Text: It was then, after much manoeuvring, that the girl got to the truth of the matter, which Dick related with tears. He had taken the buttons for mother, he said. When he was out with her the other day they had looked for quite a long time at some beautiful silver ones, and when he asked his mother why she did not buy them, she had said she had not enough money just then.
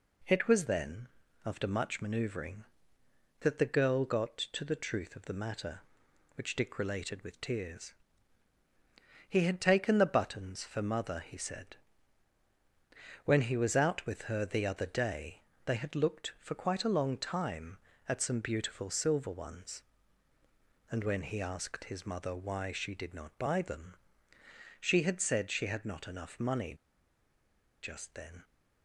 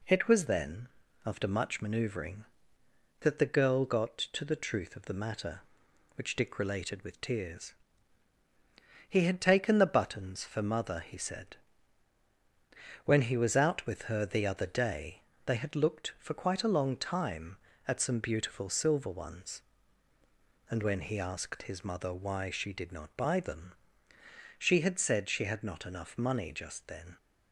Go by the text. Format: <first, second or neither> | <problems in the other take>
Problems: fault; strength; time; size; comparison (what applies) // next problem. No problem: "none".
second | pauses between "day" and "they"; slight; at 15.4 s; 0.24 s long; slight in the second // pauses between "money" and "just"; at 26.7 s; 1.0 s long